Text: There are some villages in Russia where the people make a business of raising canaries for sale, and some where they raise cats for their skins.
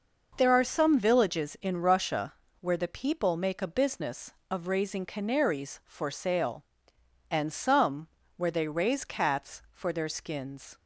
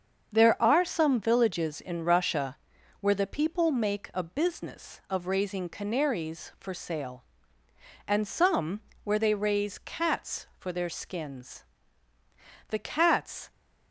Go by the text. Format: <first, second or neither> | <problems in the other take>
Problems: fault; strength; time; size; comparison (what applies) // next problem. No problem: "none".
first | starts louder than the rest; strong; until 1.3 s; 7 dB // pauses between "Russia" and "where"; at 2.5 s; 0.44 s long; slight in the first // pauses between "some" and "where"; slight; at 8.8 s; 0.24 s long; slight in the first // goes on to say "The cats"; noticeable; from 12.7 s on; 0.80 s long